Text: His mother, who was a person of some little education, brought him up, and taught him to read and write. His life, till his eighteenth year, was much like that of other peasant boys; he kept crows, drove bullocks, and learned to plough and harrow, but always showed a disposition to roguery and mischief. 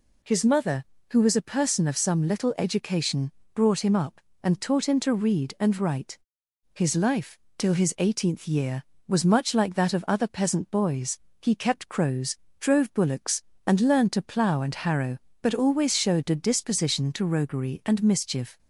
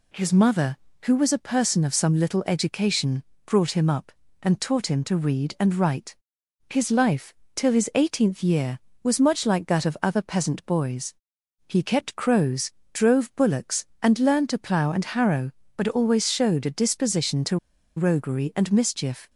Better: first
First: none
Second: pauses between "to" and "roguery"; at 17.5 s; 0.40 s long

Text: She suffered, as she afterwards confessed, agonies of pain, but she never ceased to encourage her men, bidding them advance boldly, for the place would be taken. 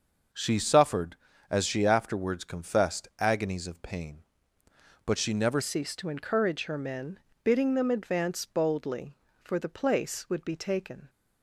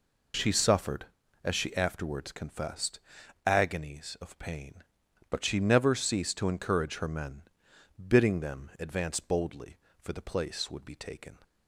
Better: second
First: starts louder than the rest; noticeable; until 1.6 s; 6 dB // changes voice at "ceased"; from 5.6 s on; 5.4 s long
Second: none

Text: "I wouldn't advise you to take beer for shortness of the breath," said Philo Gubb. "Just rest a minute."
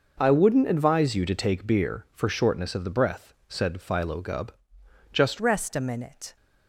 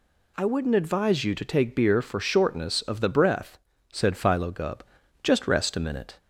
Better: second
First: changes voice at "rest"; from 5.3 s on; 1.0 s long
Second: none

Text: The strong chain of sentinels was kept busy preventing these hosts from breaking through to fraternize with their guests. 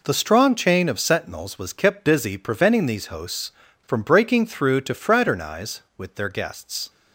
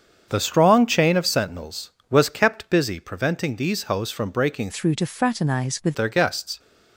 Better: first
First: none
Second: starts louder than the rest; strong; until 1.2 s; 7 dB // changes voice from "through" to "with"; from 4.7 to 5.9 s; 1.2 s long

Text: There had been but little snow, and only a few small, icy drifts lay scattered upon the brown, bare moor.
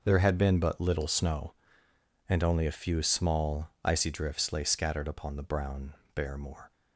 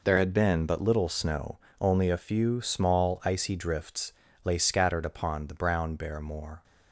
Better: first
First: none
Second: skips "and"; at 1.6 s // pauses between "drifts" and "lay"; slight; at 4.1 s; 0.32 s long

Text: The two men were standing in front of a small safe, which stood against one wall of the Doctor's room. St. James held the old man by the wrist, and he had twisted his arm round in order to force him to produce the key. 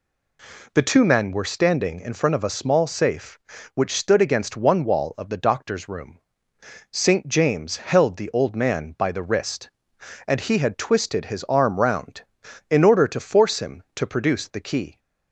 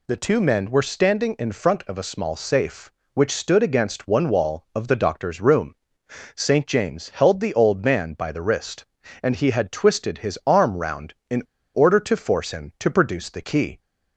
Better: first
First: none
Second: pauses between "in" and "order"; slight; at 11.4 s; 0.31 s long

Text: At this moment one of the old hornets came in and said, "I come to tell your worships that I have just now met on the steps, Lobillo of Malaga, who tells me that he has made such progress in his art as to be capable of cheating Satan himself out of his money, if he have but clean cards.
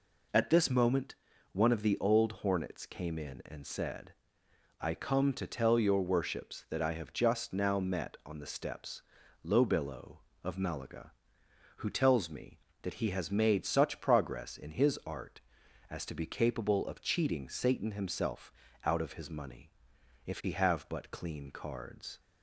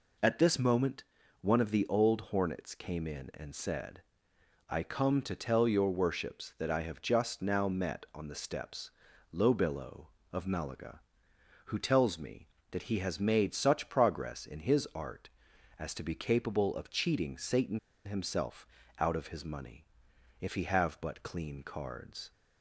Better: first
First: pauses between "moment" and "one"; at 1.1 s; 0.38 s long // pauses between "himself" and "out"; slight; at 18.5 s; 0.32 s long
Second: pauses between "moment" and "one"; at 1.0 s; 0.38 s long // pauses between "Satan" and "himself"; slight; at 17.7 s; 0.28 s long // pauses between "himself" and "out"; slight; at 18.6 s; 0.32 s long

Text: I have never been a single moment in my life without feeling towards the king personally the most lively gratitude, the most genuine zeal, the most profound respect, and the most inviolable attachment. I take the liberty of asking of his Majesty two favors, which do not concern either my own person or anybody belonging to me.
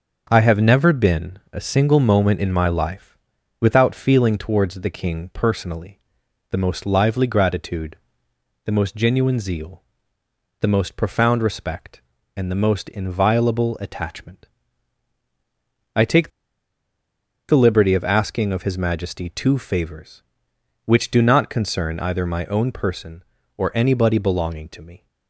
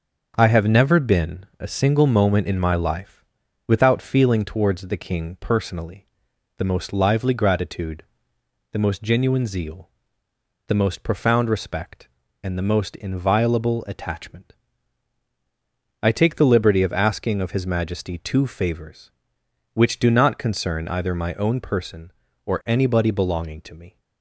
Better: second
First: starts louder than the rest; until 1.3 s; 6.5 dB // pauses between "been" and "a"; slight; at 1.3 s; 0.16 s long // pauses between "life" and "without"; noticeable; at 3.1 s; 0.46 s long // pauses between "personally" and "the"; noticeable; at 6.0 s; 0.50 s long // pauses between "take" and "the"; at 16.2 s; 1.2 s long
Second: starts louder than the rest; until 1.3 s; 6.5 dB // pauses between "been" and "a"; slight; at 1.4 s; 0.16 s long // pauses between "life" and "without"; noticeable; at 3.2 s; 0.46 s long // pauses between "personally" and "the"; noticeable; at 6.0 s; 0.50 s long

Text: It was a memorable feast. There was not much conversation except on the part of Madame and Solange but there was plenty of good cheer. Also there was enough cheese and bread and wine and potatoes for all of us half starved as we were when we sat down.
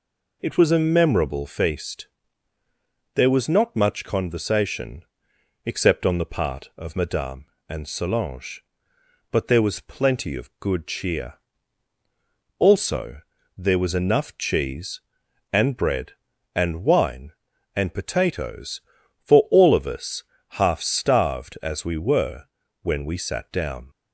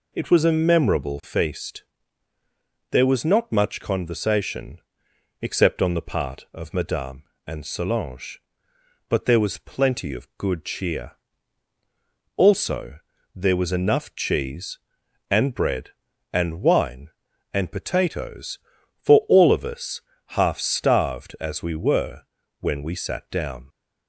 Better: neither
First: pauses between "conversation" and "except"; noticeable; at 5.0 s; 0.64 s long // pauses between "Also" and "there"; slight; at 13.2 s; 0.36 s long // pauses between "us" and "half"; slight; at 20.2 s; 0.28 s long // pauses between "were" and "when"; at 22.4 s; 0.38 s long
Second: pauses between "conversation" and "except"; noticeable; at 4.7 s; 0.64 s long // pauses between "Also" and "there"; slight; at 12.9 s; 0.36 s long // pauses between "us" and "half"; slight; at 20.0 s; 0.28 s long // pauses between "were" and "when"; at 22.2 s; 0.38 s long

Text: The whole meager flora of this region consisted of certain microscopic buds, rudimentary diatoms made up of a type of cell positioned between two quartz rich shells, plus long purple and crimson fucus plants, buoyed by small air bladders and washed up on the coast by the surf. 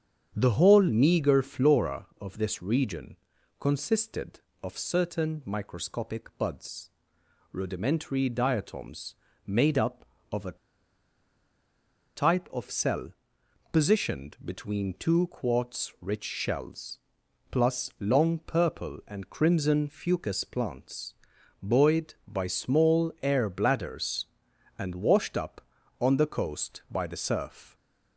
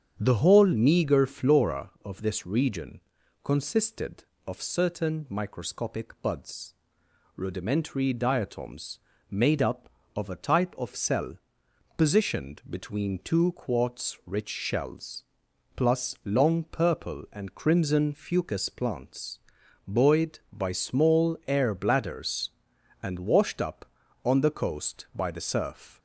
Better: second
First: starts louder than the rest; strong; until 1.3 s; 8 dB // pauses between "region" and "consisted"; at 3.1 s; 0.42 s long // pauses between "diatoms" and "made"; slight; at 9.1 s; 0.32 s long // pauses between "a" and "type"; strong; at 10.5 s; 1.5 s long // pauses between "cell" and "positioned"; noticeable; at 13.1 s; 0.62 s long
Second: starts louder than the rest; strong; until 1.2 s; 8 dB // pauses between "region" and "consisted"; at 3.0 s; 0.42 s long // pauses between "diatoms" and "made"; slight; at 8.9 s; 0.32 s long // pauses between "cell" and "positioned"; noticeable; at 11.3 s; 0.62 s long

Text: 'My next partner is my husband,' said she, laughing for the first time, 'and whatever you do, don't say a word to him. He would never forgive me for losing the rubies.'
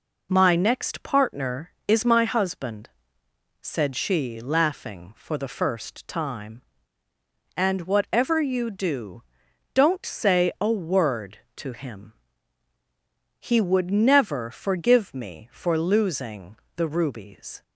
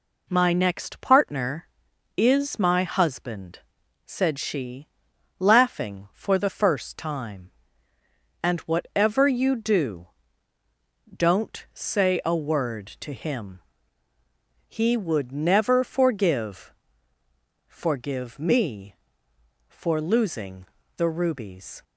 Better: first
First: pauses between "losing" and "the"; slight; at 16.5 s; 0.20 s long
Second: says "forgive" twice; at 17.6 s // pauses between "losing" and "the"; slight; at 20.6 s; 0.32 s long

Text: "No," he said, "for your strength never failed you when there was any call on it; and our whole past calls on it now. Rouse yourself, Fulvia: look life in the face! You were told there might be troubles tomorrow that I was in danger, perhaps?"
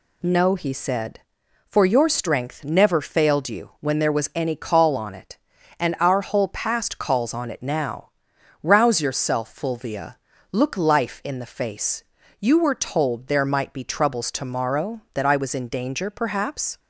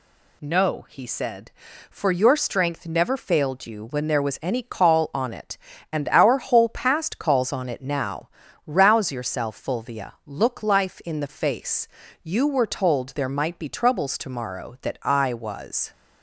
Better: first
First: none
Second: stops before "in danger perhaps"; at 15.9 s

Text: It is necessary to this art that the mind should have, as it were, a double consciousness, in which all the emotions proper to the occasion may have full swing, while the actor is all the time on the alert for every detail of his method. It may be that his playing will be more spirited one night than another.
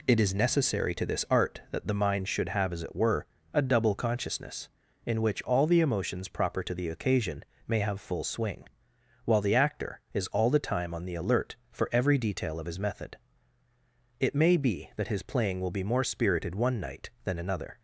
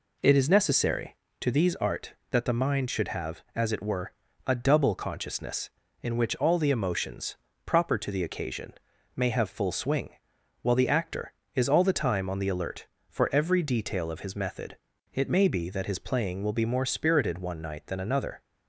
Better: first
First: pauses between "occasion" and "may"; slight; at 7.4 s; 0.22 s long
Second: says "these" for "this"; at 1.5 s // pauses between "emotions" and "proper"; slight; at 7.3 s; 0.30 s long // pauses between "occasion" and "may"; at 8.7 s; 0.42 s long

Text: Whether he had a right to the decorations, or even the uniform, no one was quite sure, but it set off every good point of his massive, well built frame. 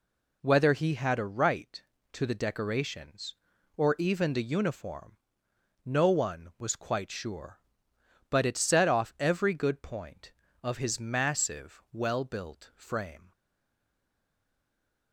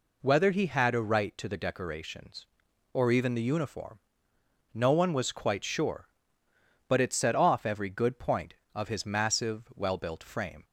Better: second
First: stays silent after the last word; noticeable; from 13.3 s on; 1.8 s long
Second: none

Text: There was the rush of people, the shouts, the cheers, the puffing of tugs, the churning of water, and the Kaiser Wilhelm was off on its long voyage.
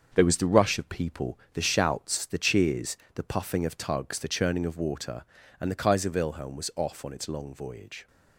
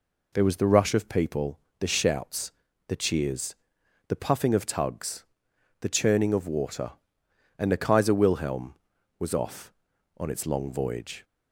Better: second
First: gets quieter; throughout; 7 dB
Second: none

